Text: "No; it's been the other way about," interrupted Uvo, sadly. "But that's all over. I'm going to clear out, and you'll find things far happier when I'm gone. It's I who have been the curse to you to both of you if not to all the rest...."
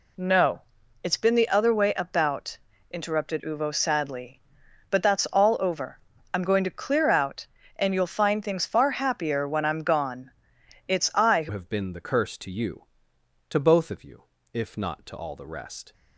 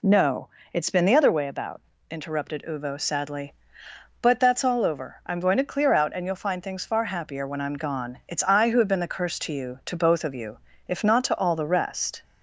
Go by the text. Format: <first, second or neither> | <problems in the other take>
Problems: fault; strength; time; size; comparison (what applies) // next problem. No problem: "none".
second | changes voice at "have"; from 11.5 s on; 4.4 s long // pauses between "you" and "if"; slight; at 14.2 s; 0.32 s long; slight in the second